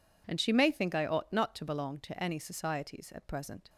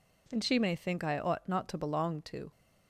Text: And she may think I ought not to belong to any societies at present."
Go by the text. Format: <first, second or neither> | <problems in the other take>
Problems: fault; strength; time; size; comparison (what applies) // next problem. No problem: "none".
first | stops before "any societies at present"; at 2.5 s